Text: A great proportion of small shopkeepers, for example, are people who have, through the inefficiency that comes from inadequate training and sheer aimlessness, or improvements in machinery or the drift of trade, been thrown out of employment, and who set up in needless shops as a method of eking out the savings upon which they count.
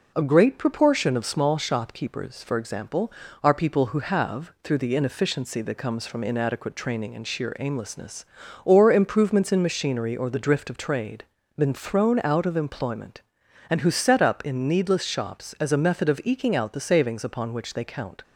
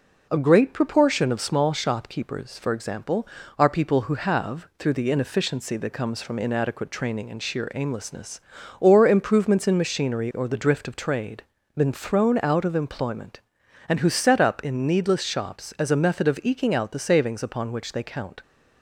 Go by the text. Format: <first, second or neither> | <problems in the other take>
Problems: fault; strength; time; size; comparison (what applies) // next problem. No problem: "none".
neither | none